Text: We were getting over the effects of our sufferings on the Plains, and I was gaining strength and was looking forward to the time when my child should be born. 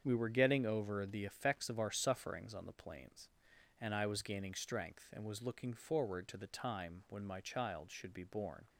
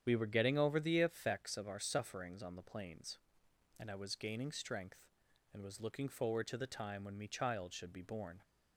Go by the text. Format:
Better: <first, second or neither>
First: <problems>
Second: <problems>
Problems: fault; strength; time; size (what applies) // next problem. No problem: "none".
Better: first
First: starts louder than the rest; strong; until 1.0 s; 7.5 dB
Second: starts louder than the rest; strong; until 1.0 s; 9 dB // says "me" for "my"; at 7.1 s